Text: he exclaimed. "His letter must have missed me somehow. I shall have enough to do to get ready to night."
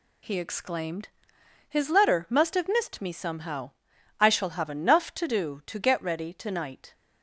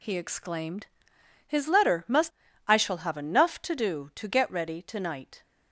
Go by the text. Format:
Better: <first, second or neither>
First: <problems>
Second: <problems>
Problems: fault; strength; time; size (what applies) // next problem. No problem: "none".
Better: first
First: none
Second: skips "have missed me somehow"; at 2.4 s